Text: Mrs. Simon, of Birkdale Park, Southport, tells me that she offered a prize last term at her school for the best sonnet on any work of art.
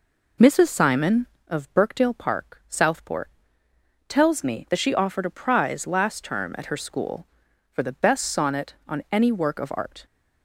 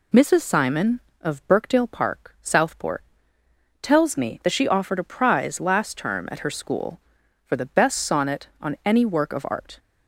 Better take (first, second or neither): second